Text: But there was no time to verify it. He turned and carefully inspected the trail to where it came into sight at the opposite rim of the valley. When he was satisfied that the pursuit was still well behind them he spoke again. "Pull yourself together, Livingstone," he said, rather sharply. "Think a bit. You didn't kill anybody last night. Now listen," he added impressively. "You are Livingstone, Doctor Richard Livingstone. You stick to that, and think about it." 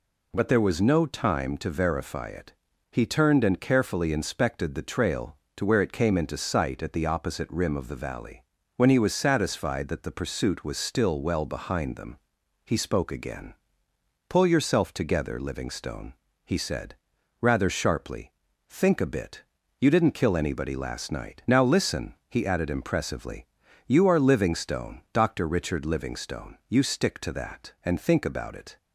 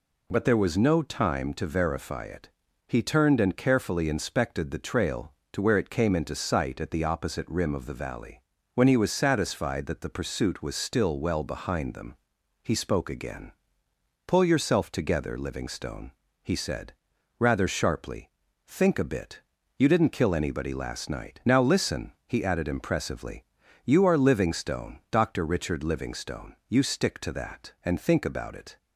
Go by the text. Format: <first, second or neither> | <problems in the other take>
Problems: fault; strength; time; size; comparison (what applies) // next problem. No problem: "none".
neither | pauses between "them" and "he"; noticeable; the same in both